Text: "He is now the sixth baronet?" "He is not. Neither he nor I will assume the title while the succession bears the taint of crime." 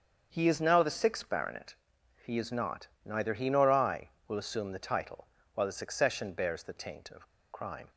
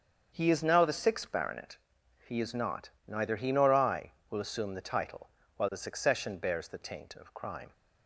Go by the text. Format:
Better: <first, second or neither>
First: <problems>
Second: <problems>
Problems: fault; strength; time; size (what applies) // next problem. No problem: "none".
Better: second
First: starts louder than the rest; strong; until 1.3 s; 7 dB // pauses between "title" and "while"; slight; at 5.2 s; 0.28 s long // pauses between "of" and "crime"; slight; at 7.2 s; 0.25 s long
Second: starts louder than the rest; strong; until 1.3 s; 7 dB // pauses between "title" and "while"; slight; at 5.2 s; 0.28 s long